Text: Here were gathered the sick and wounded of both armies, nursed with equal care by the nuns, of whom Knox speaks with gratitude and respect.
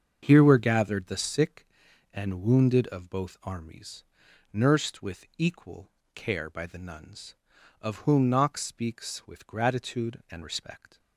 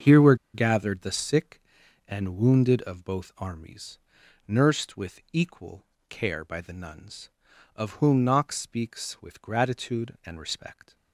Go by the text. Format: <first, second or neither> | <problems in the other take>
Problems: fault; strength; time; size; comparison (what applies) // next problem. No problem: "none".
first | starts louder than the rest; until 1.2 s; 7 dB; also in the first // pauses between "were" and "gathered"; slight; at 0.3 s; 0.18 s long // pauses between "equal" and "care"; slight; at 5.8 s; 0.26 s long; slight in the first